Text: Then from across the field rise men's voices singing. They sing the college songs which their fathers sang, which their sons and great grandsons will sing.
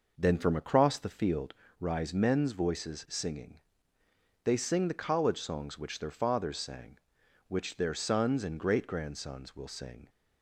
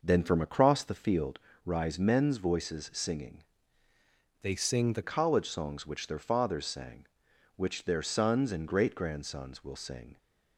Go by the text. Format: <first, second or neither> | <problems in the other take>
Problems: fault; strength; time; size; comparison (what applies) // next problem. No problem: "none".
first | pauses between "field" and "rise"; slight; at 1.3 s; 0.26 s long; slight in the first // changes voice from "They" to "the"; from 4.4 to 5.0 s; 0.6 s long